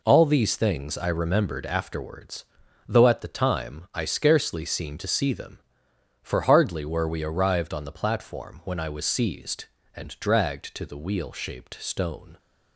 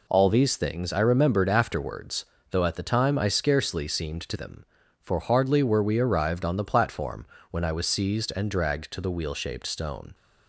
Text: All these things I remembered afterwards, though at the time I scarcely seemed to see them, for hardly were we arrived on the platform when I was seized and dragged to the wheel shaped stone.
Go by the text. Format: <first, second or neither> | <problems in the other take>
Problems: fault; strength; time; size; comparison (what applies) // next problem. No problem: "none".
first | skips "see"; at 4.3 s // pauses between "platform" and "when"; slight; at 7.2 s; 0.24 s long